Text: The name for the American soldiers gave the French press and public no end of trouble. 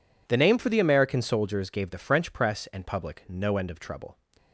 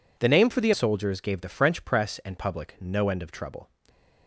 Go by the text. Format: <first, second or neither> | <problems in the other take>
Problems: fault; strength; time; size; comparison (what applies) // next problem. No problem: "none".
first | skips "American"; at 0.7 s